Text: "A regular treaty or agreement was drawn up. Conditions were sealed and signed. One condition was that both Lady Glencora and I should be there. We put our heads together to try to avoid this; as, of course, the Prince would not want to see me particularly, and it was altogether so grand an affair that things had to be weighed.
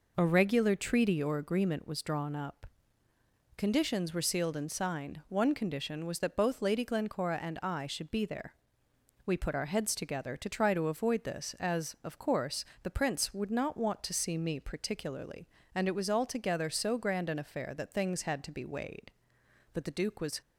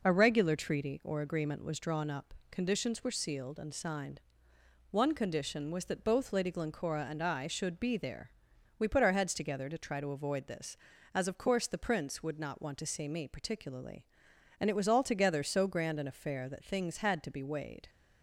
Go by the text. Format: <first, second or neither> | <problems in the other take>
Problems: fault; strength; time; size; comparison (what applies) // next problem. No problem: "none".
second | goes on to say "But the Duke was"; noticeable; from 19.7 s on; 0.68 s long